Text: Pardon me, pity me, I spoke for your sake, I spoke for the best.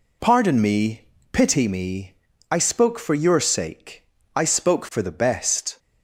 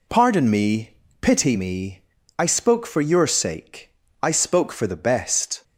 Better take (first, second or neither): neither